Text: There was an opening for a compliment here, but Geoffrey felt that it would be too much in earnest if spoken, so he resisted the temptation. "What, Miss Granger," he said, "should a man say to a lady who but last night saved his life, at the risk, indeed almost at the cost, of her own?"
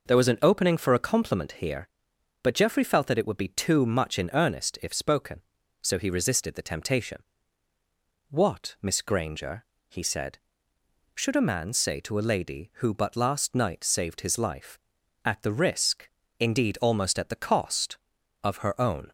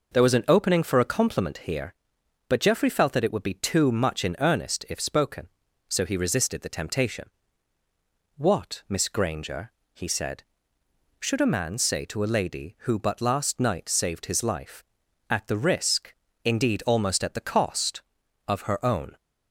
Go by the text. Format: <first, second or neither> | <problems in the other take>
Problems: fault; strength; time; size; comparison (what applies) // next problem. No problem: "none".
neither | none